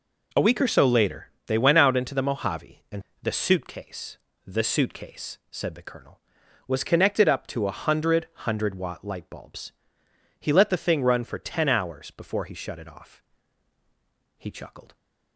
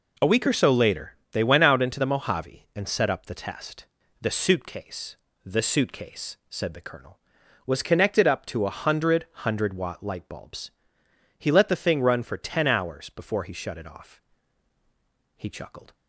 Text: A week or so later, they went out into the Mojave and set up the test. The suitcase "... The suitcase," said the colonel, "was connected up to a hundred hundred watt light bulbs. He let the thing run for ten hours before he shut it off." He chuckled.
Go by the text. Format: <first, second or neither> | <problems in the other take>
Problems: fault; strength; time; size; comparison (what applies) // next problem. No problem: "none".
second | skips "set up the test"; at 3.1 s // pauses between "hundred" and "hundred"; slight; at 8.2 s; 0.18 s long; slight in the second